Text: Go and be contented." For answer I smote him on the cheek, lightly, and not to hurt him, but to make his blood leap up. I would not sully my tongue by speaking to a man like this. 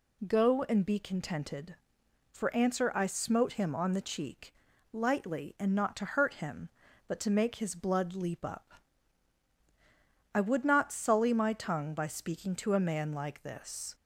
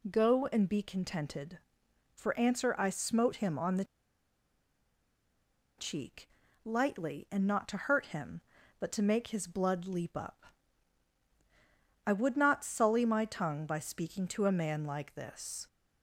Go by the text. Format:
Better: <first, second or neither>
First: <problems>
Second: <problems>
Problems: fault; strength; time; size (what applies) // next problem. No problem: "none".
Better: first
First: none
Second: pauses between "the" and "cheek"; strong; at 3.8 s; 1.9 s long